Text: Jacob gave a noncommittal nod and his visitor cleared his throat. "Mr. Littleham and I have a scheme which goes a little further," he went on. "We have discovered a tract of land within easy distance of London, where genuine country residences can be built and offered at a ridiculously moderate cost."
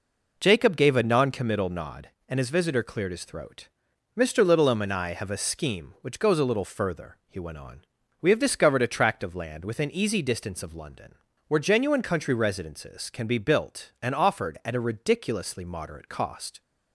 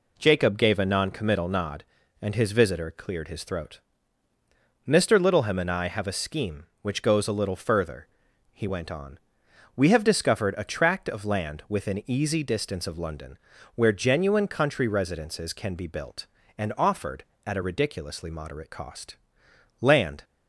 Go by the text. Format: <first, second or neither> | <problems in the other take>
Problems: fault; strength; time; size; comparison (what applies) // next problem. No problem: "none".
first | goes on to say "Land"; slight; from 19.8 s on; 0.42 s long